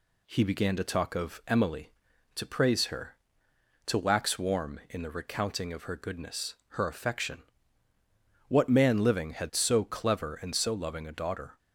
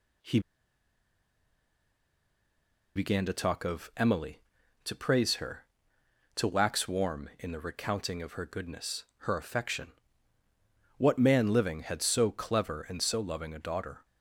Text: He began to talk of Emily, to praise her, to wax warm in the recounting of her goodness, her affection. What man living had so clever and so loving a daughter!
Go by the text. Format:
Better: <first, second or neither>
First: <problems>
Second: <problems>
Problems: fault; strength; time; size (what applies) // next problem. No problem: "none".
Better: first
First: none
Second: pauses between "He" and "began"; strong; at 0.3 s; 2.5 s long